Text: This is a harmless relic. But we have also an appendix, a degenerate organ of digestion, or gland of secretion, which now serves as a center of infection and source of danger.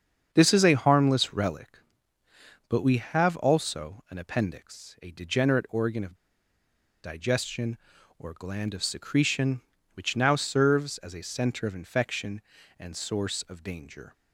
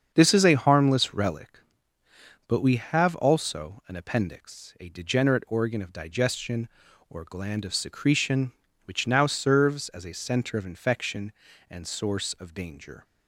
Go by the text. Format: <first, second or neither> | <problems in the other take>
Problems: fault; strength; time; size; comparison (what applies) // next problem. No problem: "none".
second | starts louder than the rest; until 1.3 s; 7 dB; strong in the second // pauses between "of" and "digestion"; noticeable; at 6.1 s; 0.90 s long